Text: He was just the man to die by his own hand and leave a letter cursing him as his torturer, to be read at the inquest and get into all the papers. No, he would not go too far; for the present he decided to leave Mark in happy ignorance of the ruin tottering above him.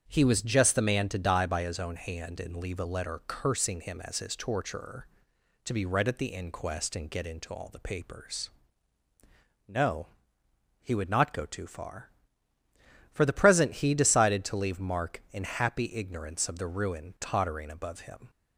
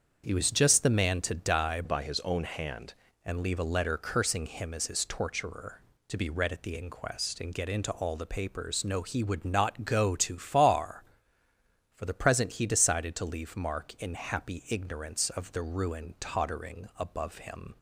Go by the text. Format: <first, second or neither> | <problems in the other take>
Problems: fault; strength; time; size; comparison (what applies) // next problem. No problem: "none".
first | starts louder than the rest; strong; until 1.2 s; 7 dB; strong in the first // changes voice from "by" to "hand"; from 1.8 to 2.9 s; 1.1 s long